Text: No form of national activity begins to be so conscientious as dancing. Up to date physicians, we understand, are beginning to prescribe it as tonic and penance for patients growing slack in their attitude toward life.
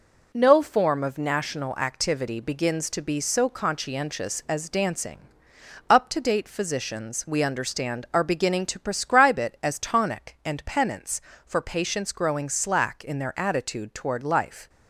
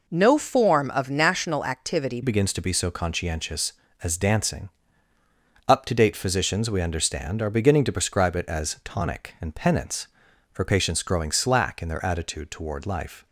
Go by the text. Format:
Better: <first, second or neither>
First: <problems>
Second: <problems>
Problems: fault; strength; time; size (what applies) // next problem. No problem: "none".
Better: first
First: none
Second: changes voice at "begins"; from 2.2 s on; 11.0 s long